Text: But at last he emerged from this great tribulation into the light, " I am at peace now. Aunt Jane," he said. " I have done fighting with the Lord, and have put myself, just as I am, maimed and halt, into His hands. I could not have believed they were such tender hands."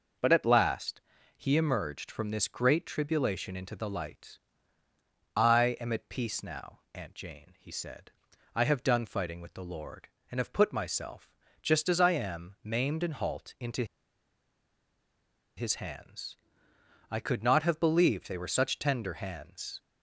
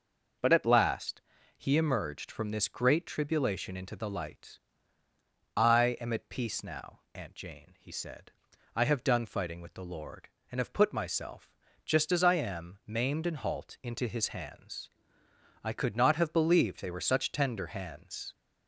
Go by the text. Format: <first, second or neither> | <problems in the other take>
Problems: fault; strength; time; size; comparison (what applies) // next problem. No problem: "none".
second | pauses between "last" and "he"; slight; at 1.0 s; 0.36 s long; slight in the second // pauses between "into" and "His"; strong; at 13.8 s; 1.7 s long